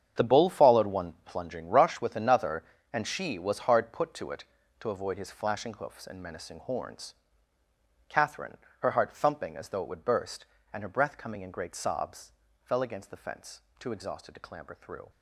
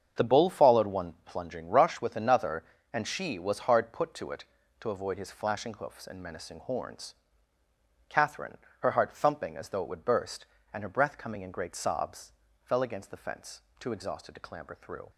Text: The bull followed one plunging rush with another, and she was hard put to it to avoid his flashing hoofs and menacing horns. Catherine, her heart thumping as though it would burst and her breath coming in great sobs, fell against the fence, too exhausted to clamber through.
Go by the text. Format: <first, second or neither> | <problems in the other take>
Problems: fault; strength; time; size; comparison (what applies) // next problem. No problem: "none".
second | gets quieter; strong; throughout; 13 dB // starts louder than the rest; strong; until 1.2 s; 8 dB; strong in the second